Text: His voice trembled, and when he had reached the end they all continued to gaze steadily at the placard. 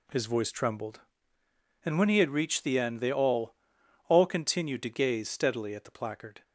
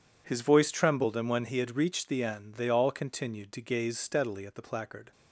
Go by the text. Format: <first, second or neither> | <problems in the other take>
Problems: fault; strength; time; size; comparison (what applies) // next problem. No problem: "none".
second | says "all" twice; at 4.0 s